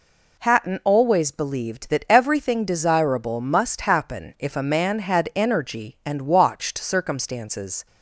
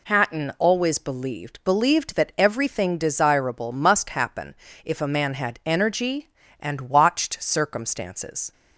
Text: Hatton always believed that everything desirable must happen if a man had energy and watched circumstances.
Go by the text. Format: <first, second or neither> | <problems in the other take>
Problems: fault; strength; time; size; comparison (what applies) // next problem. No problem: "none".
first | says "believed" twice; at 1.6 s // pauses between "happen" and "if"; slight; at 4.5 s; 0.28 s long